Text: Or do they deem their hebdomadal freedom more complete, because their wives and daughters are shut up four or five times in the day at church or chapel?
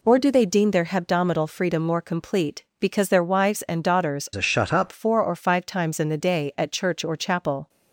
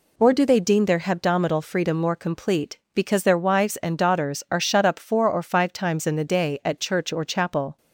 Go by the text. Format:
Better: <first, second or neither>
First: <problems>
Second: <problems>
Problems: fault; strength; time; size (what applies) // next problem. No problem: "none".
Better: second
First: changes voice from "are" to "up"; from 4.3 to 4.9 s; 0.6 s long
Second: none